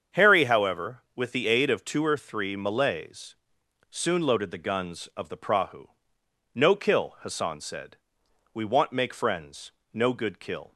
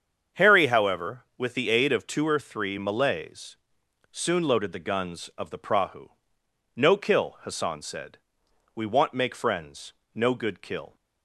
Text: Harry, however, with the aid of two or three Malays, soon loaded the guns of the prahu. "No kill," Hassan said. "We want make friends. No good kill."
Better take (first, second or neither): neither